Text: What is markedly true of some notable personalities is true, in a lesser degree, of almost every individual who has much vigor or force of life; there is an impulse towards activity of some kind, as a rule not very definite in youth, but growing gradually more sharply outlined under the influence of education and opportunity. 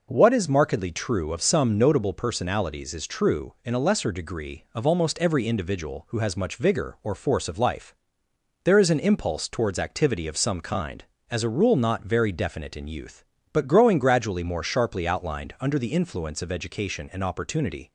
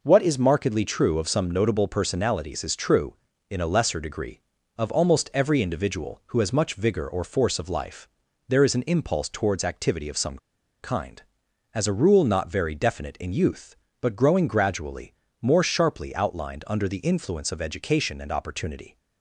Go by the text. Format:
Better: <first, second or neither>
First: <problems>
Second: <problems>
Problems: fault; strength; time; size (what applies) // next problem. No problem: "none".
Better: first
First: none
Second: pauses between "some" and "kind"; at 10.3 s; 0.43 s long // pauses between "gradually" and "more"; slight; at 15.1 s; 0.28 s long